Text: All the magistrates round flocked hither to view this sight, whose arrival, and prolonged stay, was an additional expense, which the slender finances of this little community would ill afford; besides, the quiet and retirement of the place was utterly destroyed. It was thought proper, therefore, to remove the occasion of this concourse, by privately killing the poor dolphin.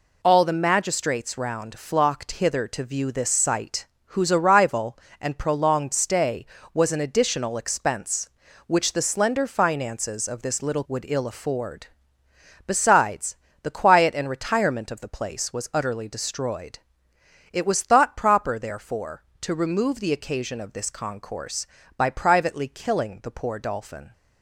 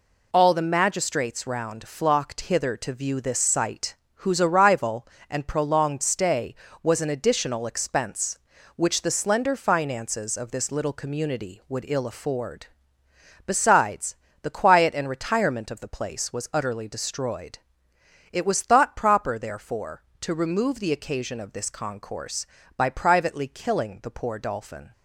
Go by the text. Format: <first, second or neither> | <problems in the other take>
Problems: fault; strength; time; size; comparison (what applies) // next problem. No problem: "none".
second | skips "community"; at 10.8 s